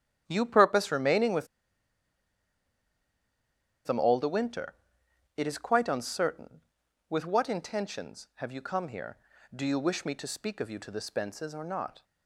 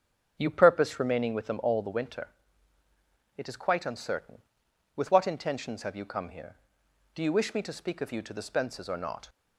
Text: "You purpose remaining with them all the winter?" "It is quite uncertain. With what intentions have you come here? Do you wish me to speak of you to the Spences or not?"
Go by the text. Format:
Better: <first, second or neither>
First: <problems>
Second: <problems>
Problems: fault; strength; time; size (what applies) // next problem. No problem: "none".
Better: second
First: starts louder than the rest; strong; until 1.2 s; 10.5 dB // pauses between "with" and "them"; strong; at 1.4 s; 2.4 s long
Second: starts louder than the rest; strong; until 1.4 s; 7 dB